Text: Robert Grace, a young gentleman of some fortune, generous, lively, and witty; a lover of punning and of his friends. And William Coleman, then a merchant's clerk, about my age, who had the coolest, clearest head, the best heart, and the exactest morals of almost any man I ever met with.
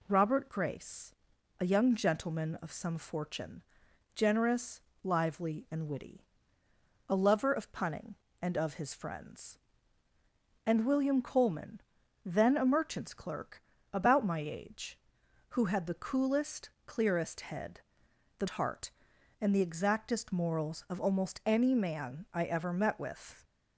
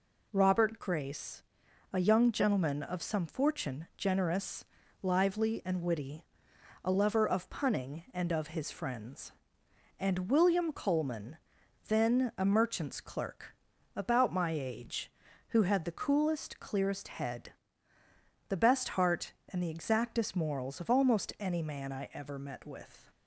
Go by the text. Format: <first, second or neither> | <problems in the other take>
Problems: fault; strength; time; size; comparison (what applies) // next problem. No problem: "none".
second | skips "best"; at 18.4 s